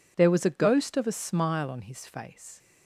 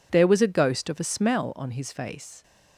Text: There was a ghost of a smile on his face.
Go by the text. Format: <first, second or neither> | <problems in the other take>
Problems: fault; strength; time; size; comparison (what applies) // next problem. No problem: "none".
first | says "smell" for "smile"; at 1.0 s